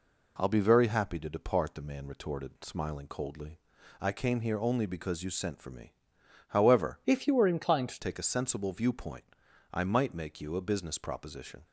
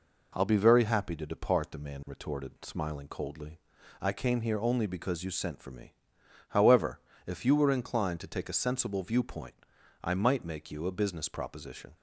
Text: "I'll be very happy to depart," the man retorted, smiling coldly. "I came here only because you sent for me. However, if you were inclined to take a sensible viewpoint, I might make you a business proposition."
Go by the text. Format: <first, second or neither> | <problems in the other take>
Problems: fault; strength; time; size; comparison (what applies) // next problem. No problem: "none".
second | changes voice from "if" to "to"; from 7.0 to 7.9 s; 0.9 s long